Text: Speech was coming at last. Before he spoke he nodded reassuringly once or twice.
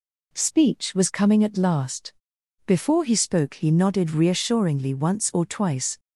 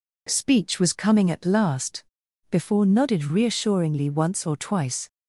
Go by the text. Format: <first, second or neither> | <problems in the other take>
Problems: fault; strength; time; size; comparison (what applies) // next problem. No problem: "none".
first | skips "he spoke he"; at 2.8 s